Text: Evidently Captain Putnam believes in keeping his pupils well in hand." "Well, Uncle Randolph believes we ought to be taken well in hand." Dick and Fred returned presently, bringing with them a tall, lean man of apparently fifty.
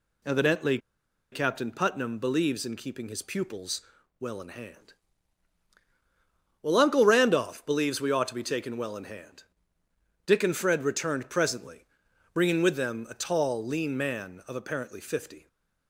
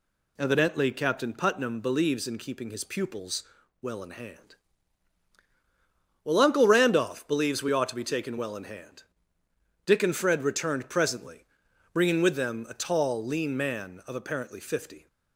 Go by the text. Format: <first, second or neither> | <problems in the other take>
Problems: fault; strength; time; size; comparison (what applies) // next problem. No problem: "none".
second | pauses between "Evidently" and "Captain"; noticeable; at 0.7 s; 0.53 s long // pauses between "pupils" and "well"; at 3.8 s; 0.38 s long; also in the second // stays silent after the last word; slight; from 15.3 s on; 0.5 s long